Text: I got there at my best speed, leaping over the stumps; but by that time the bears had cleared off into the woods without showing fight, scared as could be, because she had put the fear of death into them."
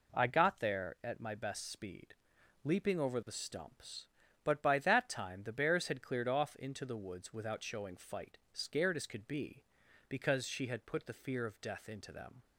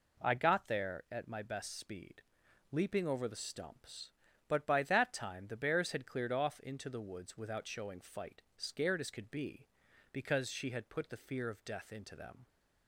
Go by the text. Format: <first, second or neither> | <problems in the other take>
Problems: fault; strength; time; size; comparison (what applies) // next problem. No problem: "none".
neither | none